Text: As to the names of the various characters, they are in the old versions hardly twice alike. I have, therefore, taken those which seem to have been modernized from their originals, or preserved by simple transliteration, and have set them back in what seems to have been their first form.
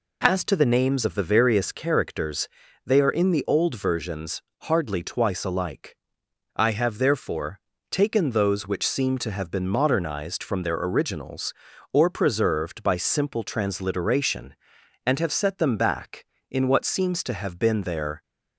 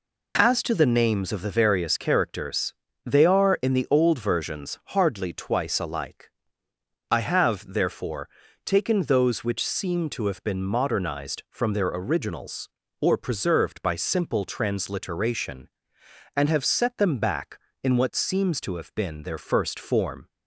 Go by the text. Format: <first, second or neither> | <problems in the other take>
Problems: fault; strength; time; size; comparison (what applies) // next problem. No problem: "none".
second | pauses between "versions" and "hardly"; slight; at 4.4 s; 0.22 s long // stops before "first form"; at 18.2 s